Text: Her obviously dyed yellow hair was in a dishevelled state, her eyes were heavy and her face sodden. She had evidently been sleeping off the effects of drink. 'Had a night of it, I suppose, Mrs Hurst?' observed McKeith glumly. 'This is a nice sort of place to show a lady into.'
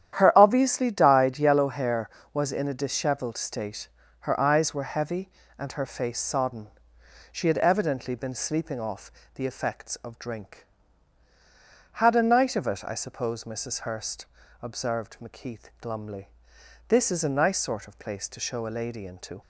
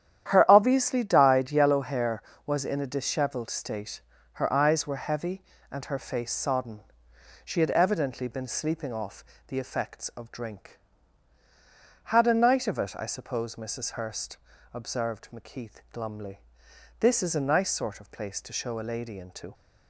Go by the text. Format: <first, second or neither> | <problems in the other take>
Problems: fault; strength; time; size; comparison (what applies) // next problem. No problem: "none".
neither | starts louder than the rest; strong; the same in both // pauses between "off" and "the"; slight; the same in both